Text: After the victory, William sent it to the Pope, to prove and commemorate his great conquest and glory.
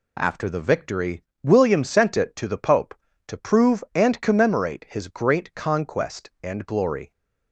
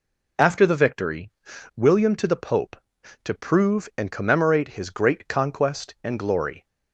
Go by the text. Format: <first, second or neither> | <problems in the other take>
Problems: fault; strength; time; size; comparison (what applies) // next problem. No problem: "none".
first | skips "sent it"; at 2.1 s